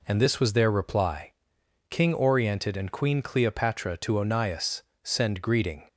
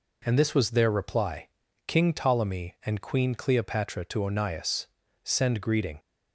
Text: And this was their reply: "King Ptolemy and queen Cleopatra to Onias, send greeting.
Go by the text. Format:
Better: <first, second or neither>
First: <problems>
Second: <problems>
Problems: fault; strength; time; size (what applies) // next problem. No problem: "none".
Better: second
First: says "Oriented" for "Ptolemy"; at 2.1 s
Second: none